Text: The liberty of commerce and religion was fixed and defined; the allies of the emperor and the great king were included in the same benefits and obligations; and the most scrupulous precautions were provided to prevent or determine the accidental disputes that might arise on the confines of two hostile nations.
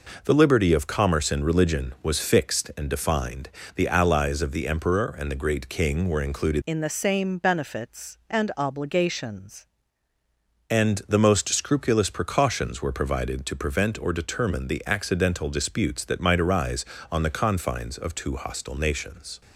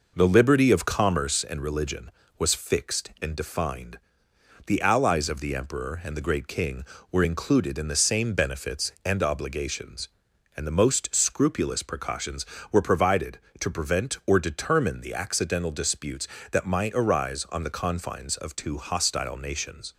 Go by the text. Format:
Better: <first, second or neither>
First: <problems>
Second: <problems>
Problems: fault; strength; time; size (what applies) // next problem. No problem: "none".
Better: second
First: changes voice from "in" to "obligations"; from 6.6 to 9.6 s; 3.0 s long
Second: none